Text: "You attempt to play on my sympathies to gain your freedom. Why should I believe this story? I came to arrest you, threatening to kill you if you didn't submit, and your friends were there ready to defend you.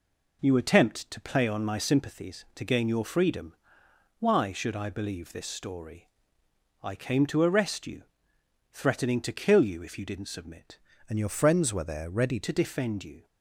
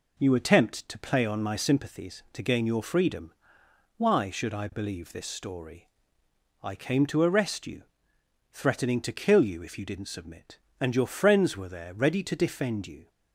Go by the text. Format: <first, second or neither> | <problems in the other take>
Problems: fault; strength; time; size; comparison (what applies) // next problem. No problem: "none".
second | changes voice from "and" to "ready"; from 11.0 to 12.4 s; 1.4 s long